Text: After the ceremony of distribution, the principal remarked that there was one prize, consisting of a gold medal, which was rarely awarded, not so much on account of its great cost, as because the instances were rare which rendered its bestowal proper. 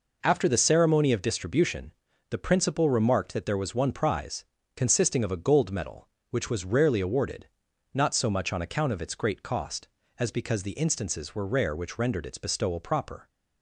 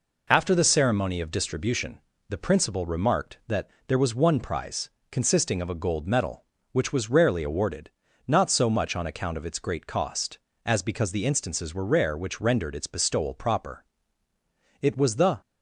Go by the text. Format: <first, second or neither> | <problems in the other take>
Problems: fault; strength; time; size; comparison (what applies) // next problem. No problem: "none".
first | pauses between "that" and "there"; slight; at 3.6 s; 0.18 s long // goes on to say "It was the"; from 14.8 s on; 0.58 s long